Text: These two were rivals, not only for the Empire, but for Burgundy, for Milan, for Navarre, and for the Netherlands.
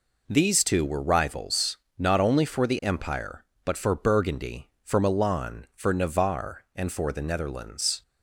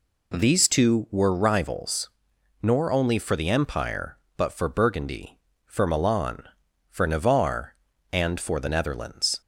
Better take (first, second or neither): first